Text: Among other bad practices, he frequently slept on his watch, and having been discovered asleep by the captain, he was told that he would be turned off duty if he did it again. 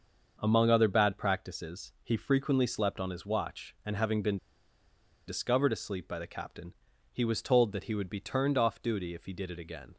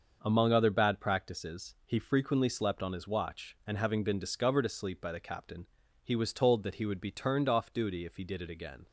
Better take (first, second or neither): second